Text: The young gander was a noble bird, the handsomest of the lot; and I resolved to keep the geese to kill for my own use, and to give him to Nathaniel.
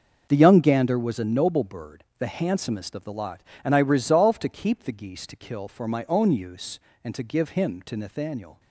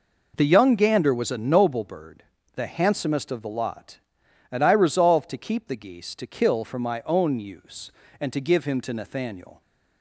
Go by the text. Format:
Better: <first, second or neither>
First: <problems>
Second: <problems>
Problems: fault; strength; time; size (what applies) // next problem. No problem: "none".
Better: neither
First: none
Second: none